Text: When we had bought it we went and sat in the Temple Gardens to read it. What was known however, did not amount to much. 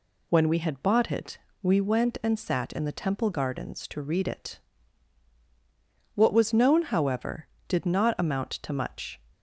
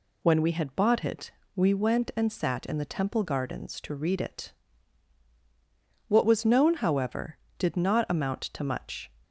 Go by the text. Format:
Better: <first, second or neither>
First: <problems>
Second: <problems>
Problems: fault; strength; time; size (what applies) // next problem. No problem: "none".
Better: neither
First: pauses between "it" and "we"; slight; at 1.3 s; 0.24 s long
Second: pauses between "it" and "we"; slight; at 1.3 s; 0.24 s long